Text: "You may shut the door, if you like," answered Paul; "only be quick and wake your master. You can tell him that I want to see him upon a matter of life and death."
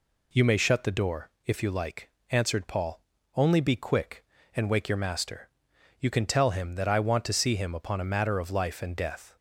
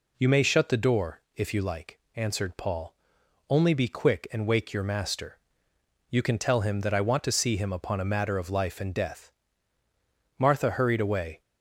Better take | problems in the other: first | goes on to say "Martha hurried away"; noticeable; from 10.3 s on; 1.0 s long

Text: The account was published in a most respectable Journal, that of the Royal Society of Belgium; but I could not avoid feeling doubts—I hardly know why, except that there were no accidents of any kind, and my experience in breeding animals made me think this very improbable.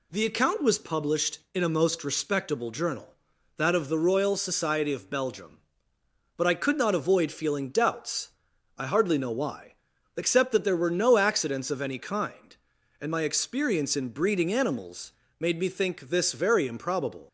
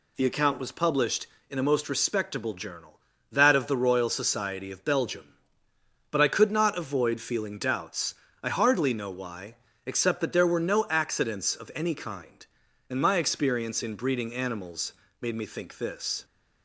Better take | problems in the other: first | pauses between "animals" and "made"; slight; at 14.9 s; 0.26 s long; slight in the first // stops before "very improbable"; at 16.2 s

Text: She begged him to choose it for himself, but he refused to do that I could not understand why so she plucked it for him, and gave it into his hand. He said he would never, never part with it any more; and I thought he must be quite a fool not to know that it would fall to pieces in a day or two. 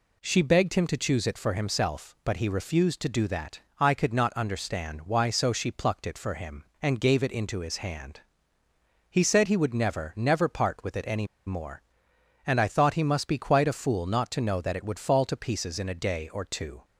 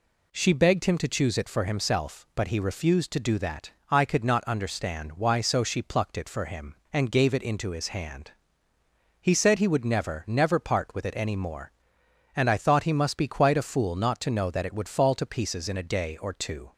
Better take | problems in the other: second | pauses between "that" and "I"; slight; at 3.6 s; 0.18 s long; slight in the second // pauses between "any" and "more"; slight; at 11.2 s; 0.19 s long

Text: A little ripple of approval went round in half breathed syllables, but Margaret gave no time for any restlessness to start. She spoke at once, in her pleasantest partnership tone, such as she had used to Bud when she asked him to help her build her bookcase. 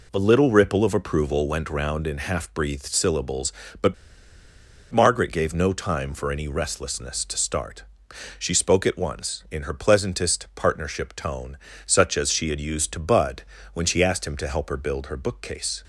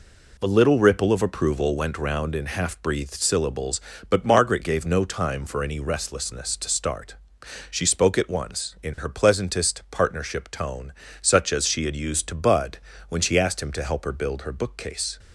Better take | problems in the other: second | pauses between "but" and "Margaret"; noticeable; at 3.9 s; 0.96 s long // pauses between "Bud" and "when"; slight; at 13.4 s; 0.30 s long; slight in the second

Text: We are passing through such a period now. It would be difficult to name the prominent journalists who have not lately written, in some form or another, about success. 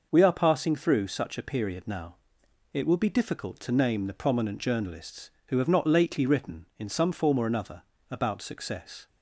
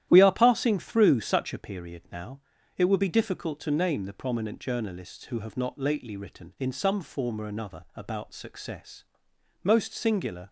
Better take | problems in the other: first | starts louder than the rest; strong; until 1.0 s; 12 dB // goes on to say "Most singular"; noticeable; from 9.6 s on; 0.86 s long

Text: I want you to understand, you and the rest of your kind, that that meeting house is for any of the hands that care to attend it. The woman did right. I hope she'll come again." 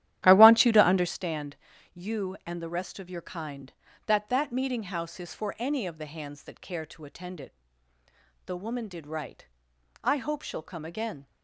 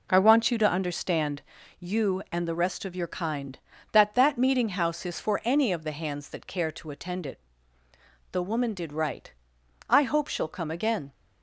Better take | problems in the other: second | starts louder than the rest; strong; until 1.1 s; 12.5 dB

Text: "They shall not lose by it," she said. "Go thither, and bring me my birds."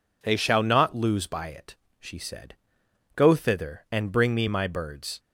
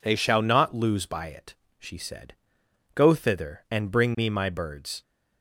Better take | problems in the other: neither | none

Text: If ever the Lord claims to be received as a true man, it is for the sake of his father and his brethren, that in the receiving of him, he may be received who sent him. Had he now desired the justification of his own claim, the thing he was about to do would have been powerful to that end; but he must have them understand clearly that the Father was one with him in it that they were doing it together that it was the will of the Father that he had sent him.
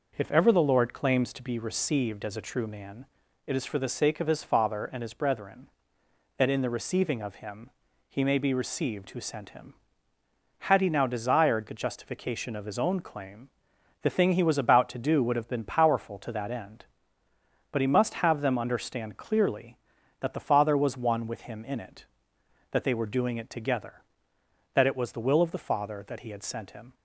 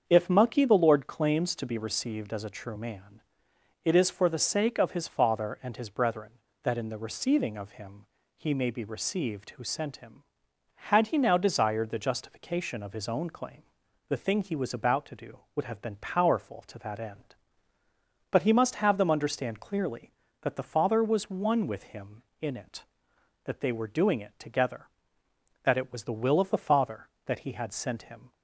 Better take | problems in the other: first | starts louder than the rest; until 1.0 s; 7 dB // says "mucky" for "ever"; at 0.2 s

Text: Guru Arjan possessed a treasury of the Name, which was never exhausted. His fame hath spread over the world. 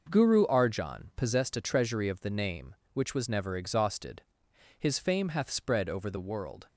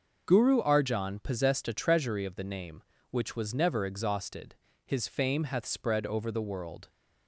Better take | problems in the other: neither | none

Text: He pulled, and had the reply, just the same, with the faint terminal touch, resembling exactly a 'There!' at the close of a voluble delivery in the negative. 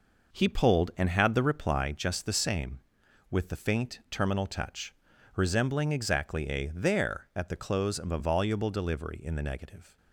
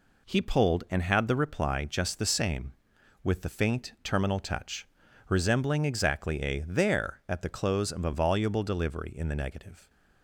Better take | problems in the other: second | starts louder than the rest; noticeable; until 2.0 s; 5 dB

